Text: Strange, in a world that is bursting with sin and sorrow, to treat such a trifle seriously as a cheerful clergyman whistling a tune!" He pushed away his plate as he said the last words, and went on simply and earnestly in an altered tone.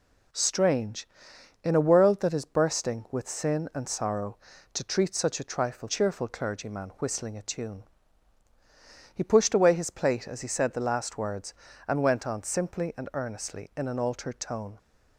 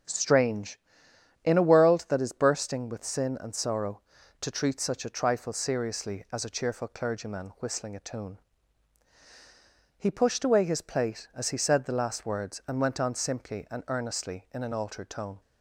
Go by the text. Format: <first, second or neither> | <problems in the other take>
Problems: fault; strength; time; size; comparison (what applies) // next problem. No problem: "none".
second | skips "seriously as a"; at 5.8 s